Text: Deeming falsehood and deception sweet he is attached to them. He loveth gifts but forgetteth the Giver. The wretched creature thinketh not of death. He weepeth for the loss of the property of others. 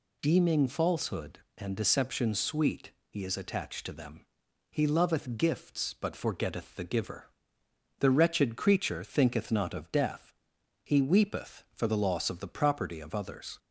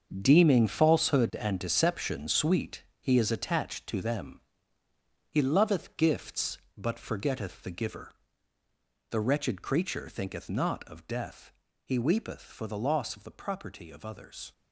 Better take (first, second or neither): first